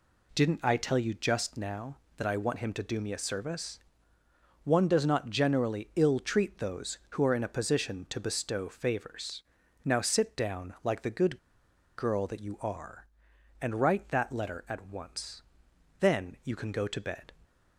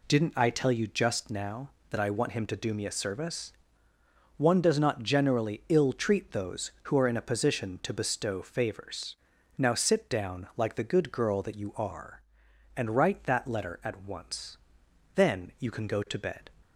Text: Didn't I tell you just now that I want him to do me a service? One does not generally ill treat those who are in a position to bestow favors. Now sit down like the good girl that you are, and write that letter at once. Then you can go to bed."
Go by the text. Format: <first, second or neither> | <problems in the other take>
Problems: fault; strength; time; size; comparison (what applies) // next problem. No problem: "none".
second | pauses between "good" and "girl"; noticeable; at 11.3 s; 0.59 s long